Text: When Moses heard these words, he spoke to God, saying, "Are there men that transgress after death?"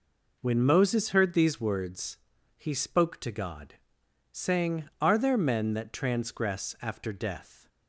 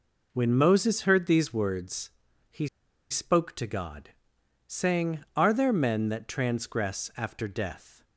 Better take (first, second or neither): first